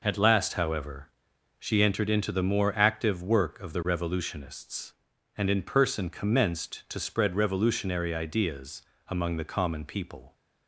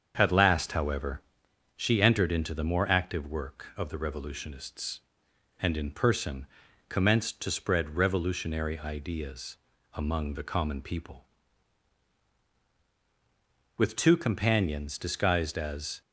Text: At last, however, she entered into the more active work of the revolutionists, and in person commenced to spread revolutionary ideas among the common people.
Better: first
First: pauses between "ideas" and "among"; slight; at 8.8 s; 0.26 s long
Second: starts louder than the rest; strong; until 1.1 s; 7 dB // pauses between "person" and "commenced"; at 6.4 s; 0.40 s long // pauses between "ideas" and "among"; slight; at 9.5 s; 0.36 s long // goes on to say "With two companions disguised as"; strong; from 13.7 s on; 2.2 s long

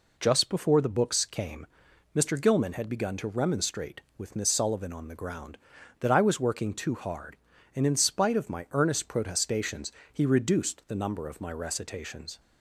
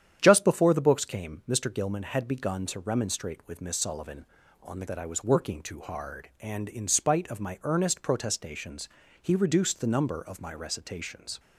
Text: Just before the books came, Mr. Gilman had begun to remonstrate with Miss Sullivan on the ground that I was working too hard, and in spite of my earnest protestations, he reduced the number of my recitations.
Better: first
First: none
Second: starts louder than the rest; strong; until 1.2 s; 9.5 dB // skips "ground"; at 4.8 s

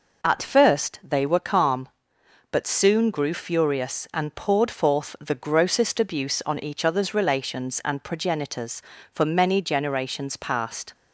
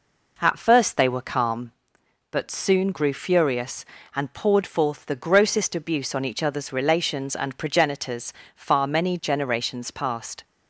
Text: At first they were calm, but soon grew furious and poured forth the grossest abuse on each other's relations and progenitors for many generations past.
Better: first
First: none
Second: says "far" for "for"; at 8.5 s

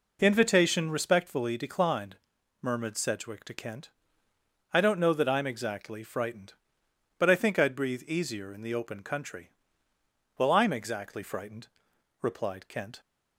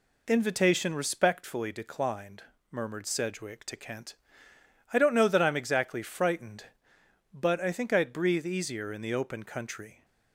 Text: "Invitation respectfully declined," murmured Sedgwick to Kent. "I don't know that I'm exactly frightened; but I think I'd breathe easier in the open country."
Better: second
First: goes on to say "Well I'm exactly frightened replied Kent"; strong; from 10.3 s on; 2.6 s long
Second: none

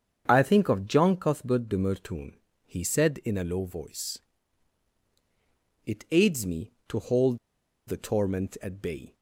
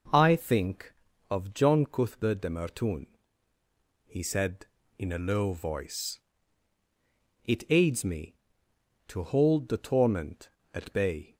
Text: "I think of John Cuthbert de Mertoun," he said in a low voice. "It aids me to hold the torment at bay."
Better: second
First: starts louder than the rest; strong; until 1.2 s; 7.5 dB // pauses between "hold" and "the"; noticeable; at 7.3 s; 0.48 s long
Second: none

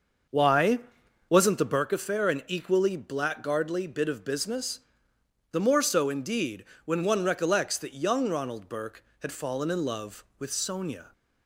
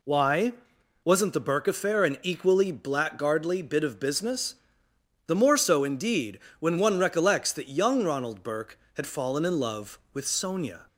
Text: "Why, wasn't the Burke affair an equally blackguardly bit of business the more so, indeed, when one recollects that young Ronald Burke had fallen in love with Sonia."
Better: second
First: starts louder than the rest; until 1.8 s; 6.5 dB // pauses between "business" and "the"; noticeable; at 4.8 s; 0.72 s long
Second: pauses between "business" and "the"; noticeable; at 4.5 s; 0.72 s long

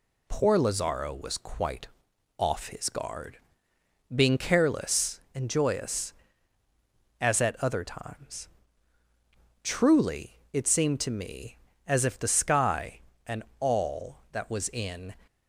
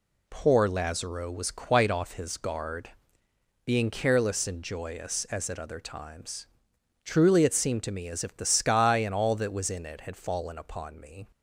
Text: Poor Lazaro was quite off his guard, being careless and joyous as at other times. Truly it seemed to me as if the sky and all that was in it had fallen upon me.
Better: second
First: pauses between "quite" and "off"; noticeable; at 1.8 s; 0.50 s long // pauses between "Truly" and "it"; slight; at 10.3 s; 0.16 s long // pauses between "and" and "all"; slight; at 13.4 s; 0.24 s long // stops before "it had fallen upon me"; at 15.2 s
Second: none

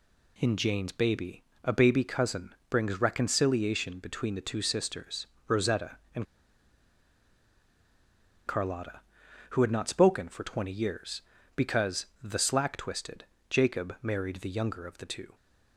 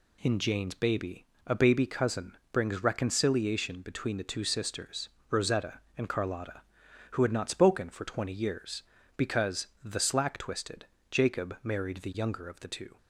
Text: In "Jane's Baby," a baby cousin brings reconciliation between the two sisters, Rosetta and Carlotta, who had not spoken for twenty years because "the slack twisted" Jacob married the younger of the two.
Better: second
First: pauses between "and" and "Carlotta"; strong; at 6.2 s; 2.2 s long // pauses between "because" and "the"; slight; at 12.0 s; 0.16 s long // pauses between "twisted" and "Jacob"; slight; at 13.2 s; 0.26 s long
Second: pauses between "because" and "the"; slight; at 9.6 s; 0.16 s long // pauses between "twisted" and "Jacob"; slight; at 10.8 s; 0.26 s long

